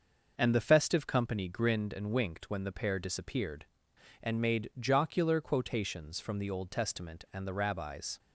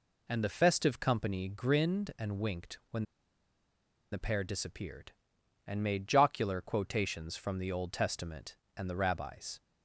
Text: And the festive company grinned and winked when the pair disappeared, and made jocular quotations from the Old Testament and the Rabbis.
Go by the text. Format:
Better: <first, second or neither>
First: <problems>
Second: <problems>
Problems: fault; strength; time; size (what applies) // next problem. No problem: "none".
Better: first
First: none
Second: pauses between "when" and "the"; at 3.0 s; 1.0 s long